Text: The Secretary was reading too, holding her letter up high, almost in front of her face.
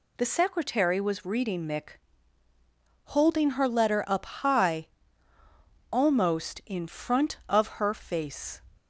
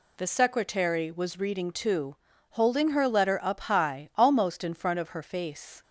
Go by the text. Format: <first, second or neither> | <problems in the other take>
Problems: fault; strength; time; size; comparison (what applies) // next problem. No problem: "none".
second | says "mick" for "too"; at 1.6 s